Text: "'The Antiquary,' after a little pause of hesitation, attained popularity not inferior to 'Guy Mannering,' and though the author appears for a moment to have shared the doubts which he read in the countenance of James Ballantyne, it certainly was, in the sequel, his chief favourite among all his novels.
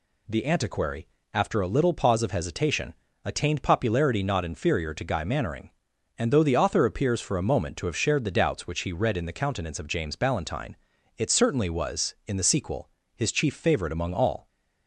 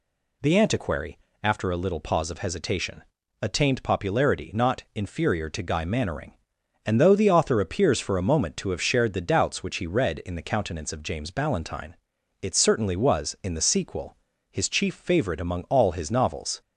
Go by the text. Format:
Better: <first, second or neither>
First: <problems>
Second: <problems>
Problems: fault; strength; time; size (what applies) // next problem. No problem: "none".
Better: second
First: stops before "his novels"; at 14.4 s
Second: none